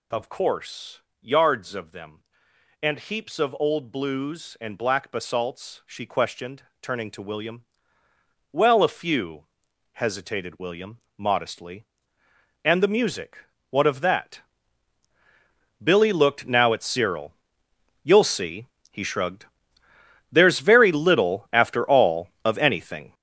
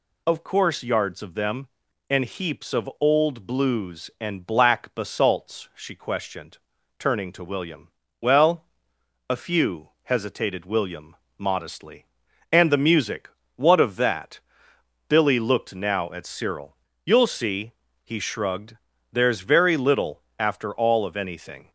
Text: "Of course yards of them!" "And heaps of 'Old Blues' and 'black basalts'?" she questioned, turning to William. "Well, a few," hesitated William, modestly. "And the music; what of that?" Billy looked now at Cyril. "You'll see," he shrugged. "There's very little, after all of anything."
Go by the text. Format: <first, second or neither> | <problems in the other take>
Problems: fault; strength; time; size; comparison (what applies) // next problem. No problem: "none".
second | gets louder; strong; throughout; 8.5 dB // pauses between "course" and "yards"; slight; at 0.9 s; 0.22 s long